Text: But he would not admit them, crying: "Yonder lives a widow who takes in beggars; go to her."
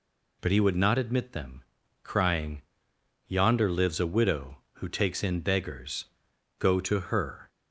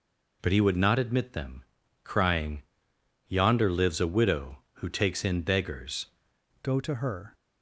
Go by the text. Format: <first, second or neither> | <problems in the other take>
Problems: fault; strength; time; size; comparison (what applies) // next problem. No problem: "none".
first | changes voice at "go"; from 6.6 s on; 0.7 s long